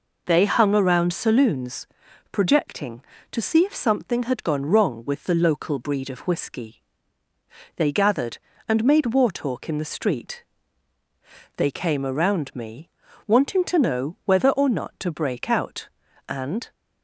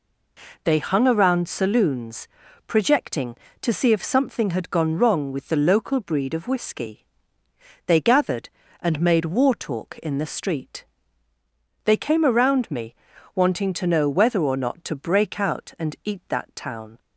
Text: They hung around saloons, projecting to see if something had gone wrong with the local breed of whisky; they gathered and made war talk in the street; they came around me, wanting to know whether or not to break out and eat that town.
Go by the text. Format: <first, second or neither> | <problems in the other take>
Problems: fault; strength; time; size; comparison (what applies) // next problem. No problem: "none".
second | stops before "eat that town"; at 16.7 s